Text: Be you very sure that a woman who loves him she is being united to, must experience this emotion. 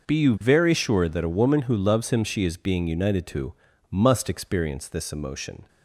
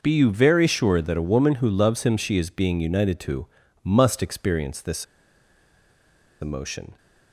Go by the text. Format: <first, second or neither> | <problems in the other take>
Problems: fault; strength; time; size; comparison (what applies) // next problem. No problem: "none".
first | pauses between "this" and "emotion"; strong; at 5.0 s; 1.3 s long